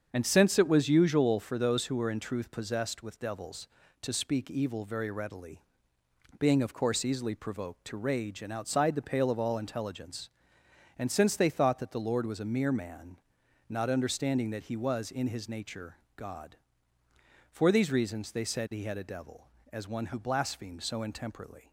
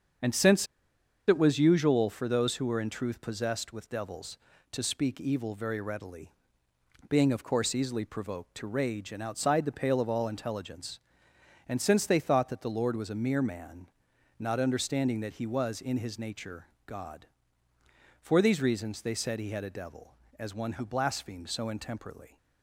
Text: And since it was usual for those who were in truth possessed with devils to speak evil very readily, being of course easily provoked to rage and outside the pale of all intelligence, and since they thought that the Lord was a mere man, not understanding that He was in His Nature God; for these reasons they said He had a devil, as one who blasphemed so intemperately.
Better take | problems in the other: first | starts louder than the rest; until 1.8 s; 7 dB; strong in the first // pauses between "since" and "it"; noticeable; at 0.6 s; 0.62 s long // pauses between "Nature" and "God"; slight; at 16.6 s; 0.18 s long; slight in the first

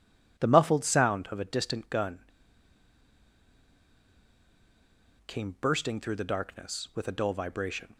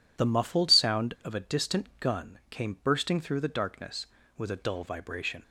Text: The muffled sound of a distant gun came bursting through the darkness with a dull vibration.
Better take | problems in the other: second | pauses between "gun" and "came"; strong; at 2.1 s; 3.0 s long

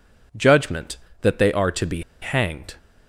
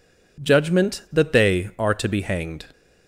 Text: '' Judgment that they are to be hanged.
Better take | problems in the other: second | pauses between "be" and "hanged"; slight; at 2.0 s; 0.20 s long

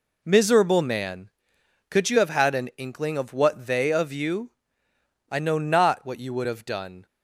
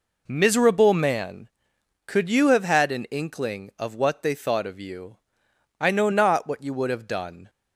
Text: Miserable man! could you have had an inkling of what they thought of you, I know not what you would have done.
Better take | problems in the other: second | skips "thought"; at 3.9 s

